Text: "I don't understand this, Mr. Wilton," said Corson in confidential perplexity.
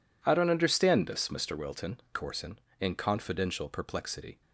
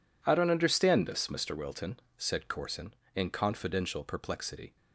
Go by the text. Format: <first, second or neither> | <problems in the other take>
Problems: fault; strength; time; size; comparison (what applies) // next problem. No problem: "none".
second | skips "said"; at 2.0 s